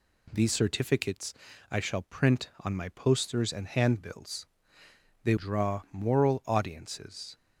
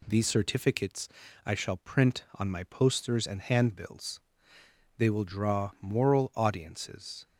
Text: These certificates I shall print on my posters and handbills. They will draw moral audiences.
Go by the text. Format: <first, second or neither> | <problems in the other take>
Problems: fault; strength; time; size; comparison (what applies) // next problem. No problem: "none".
second | pauses between "certificates" and "I"; at 1.3 s; 0.38 s long; also in the second // skips "will"; at 5.3 s